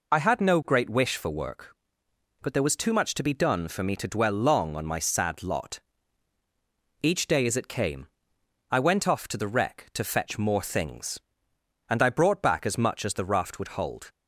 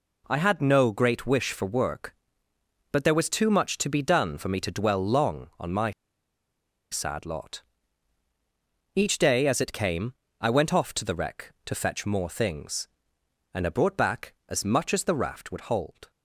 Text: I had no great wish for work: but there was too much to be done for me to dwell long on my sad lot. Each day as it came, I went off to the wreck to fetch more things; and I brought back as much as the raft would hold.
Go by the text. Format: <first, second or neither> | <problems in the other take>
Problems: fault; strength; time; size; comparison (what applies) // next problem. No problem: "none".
first | pauses between "my" and "sad"; at 5.9 s; 0.99 s long